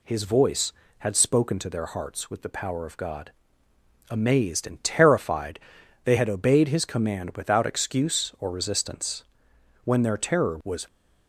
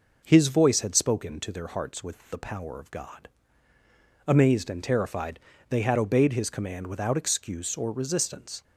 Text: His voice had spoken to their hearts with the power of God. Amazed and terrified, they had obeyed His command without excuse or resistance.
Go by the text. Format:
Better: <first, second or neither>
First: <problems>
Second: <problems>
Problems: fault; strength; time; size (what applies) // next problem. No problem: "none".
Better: second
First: goes on to say "When their terror was"; noticeable; from 9.8 s on; 1.0 s long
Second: none